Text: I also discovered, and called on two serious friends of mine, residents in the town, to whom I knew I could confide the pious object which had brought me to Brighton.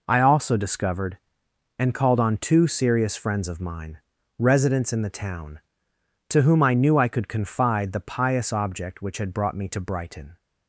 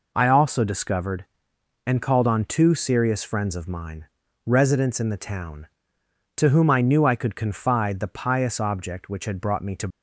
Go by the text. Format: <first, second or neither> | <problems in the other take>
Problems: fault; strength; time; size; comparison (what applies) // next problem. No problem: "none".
first | stops before "Brighton"; at 9.9 s